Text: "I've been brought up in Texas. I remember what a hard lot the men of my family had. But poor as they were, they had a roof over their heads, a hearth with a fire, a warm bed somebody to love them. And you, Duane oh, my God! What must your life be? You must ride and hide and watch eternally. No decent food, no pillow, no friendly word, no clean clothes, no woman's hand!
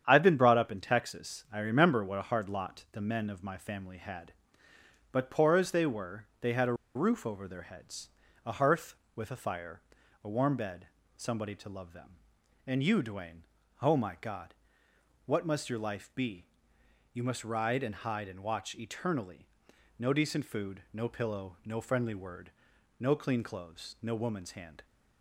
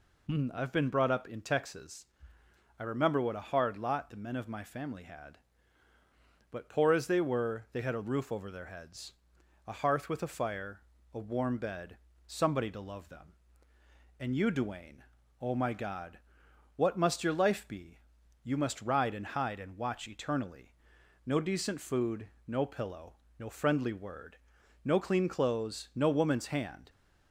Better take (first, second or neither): second